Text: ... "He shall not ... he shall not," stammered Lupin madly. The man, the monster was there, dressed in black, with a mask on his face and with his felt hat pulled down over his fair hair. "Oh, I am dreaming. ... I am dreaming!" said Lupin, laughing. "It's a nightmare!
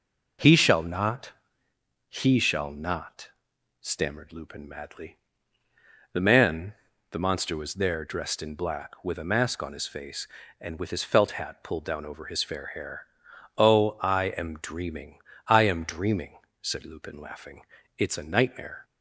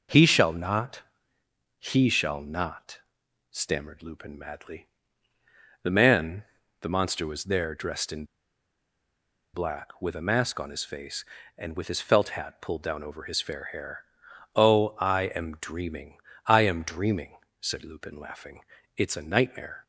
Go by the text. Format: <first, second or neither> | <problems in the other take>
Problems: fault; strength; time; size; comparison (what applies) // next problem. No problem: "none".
first | pauses between "in" and "black"; strong; at 8.2 s; 1.3 s long